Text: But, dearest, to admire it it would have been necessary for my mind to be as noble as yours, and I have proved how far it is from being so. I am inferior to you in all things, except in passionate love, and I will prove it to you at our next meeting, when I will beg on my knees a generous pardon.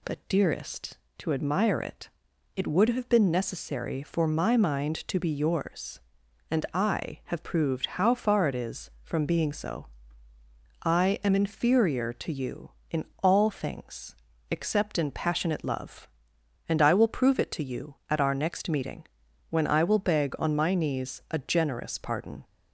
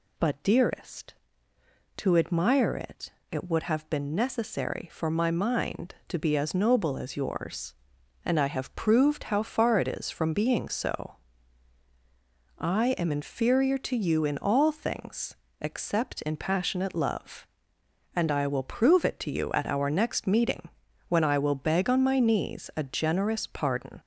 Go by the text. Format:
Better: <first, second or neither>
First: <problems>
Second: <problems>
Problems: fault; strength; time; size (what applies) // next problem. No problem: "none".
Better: second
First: pauses between "it" and "it"; noticeable; at 2.0 s; 0.46 s long // skips "as noble as"; at 5.2 s // pauses between "in" and "all"; slight; at 13.0 s; 0.18 s long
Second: pauses between "it" and "it"; slight; at 3.1 s; 0.20 s long